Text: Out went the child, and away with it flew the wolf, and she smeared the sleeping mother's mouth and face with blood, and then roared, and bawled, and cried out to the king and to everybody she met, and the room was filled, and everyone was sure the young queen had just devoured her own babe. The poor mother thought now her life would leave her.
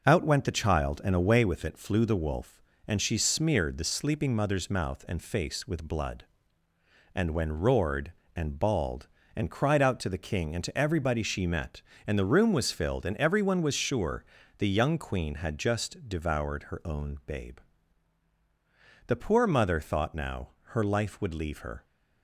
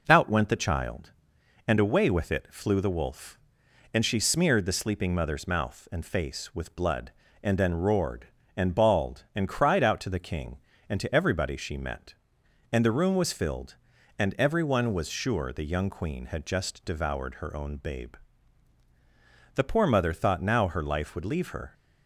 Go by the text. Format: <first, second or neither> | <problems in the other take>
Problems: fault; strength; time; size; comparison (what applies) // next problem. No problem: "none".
second | starts louder than the rest; noticeable; until 1.0 s; 6 dB // says "when" for "then"; at 7.3 s // pauses between "sure" and "the"; slight; at 14.2 s; 0.32 s long // pauses between "now" and "her"; slight; at 20.4 s; 0.20 s long